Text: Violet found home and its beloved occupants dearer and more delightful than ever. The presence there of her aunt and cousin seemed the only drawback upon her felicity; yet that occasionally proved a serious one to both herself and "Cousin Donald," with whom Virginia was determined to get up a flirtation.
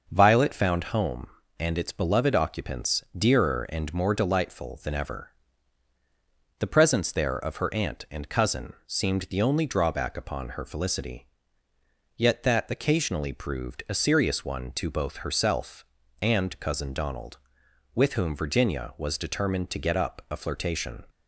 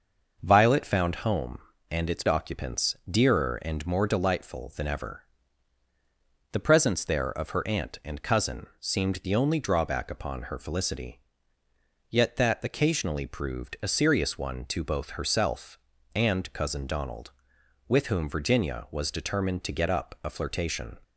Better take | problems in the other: first | starts louder than the rest; noticeable; until 1.4 s; 6 dB // skips "beloved"; at 2.2 s // pauses between "occupants" and "dearer"; slight; at 2.9 s; 0.16 s long; slight in the first

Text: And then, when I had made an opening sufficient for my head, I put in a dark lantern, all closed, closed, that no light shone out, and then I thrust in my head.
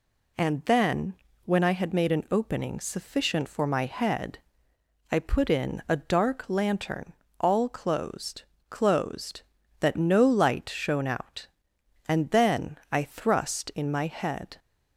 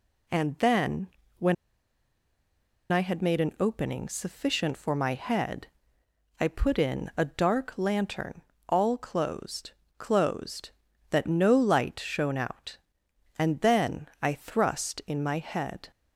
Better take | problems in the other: first | pauses between "when" and "I"; strong; at 1.5 s; 1.3 s long

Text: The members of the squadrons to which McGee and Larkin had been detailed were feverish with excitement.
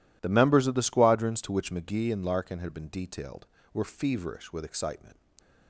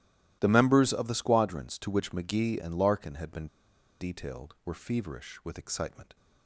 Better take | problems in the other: first | starts louder than the rest; strong; until 1.4 s; 15 dB // pauses between "been" and "detailed"; noticeable; at 3.4 s; 0.53 s long

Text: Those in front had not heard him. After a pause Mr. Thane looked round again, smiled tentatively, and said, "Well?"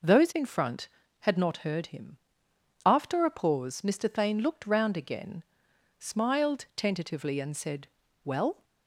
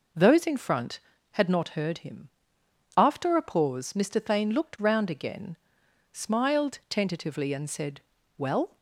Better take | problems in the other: neither | none

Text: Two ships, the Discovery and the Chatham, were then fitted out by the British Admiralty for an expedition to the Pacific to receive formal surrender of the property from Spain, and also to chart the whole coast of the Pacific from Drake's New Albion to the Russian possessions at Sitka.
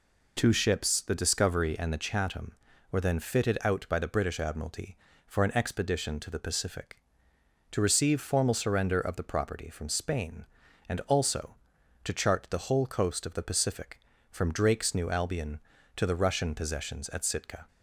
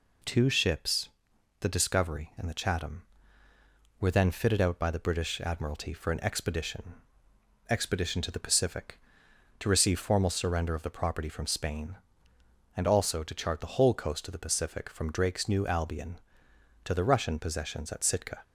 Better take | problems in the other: first | says "expedition" twice; at 7.6 s

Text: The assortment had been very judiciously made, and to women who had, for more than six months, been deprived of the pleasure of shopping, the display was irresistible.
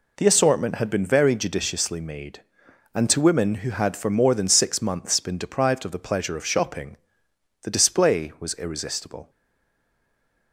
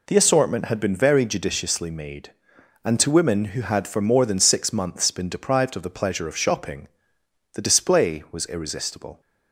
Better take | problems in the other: second | stays silent after the last word; noticeable; from 9.2 s on; 1.3 s long

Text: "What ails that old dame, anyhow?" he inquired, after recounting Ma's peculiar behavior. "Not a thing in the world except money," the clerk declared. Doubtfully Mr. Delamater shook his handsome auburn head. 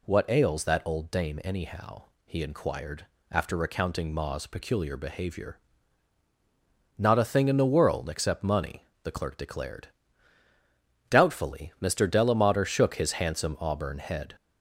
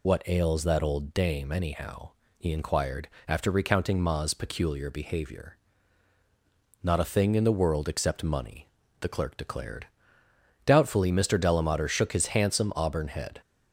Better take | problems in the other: first | loses the start of "What"; at 0.0 s; 55 ms

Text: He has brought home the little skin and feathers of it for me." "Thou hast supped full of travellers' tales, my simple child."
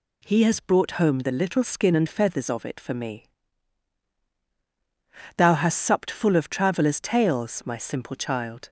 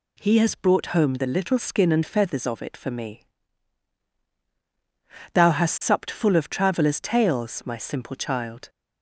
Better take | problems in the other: neither | none

